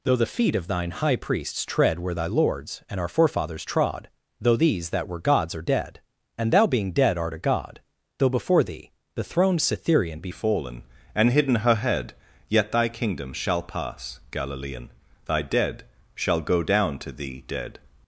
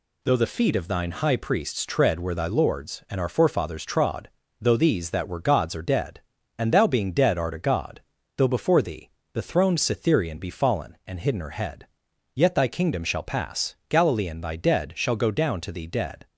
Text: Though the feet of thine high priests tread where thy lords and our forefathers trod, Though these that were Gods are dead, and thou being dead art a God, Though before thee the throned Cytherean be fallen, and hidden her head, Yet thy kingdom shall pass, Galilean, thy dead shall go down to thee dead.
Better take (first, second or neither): second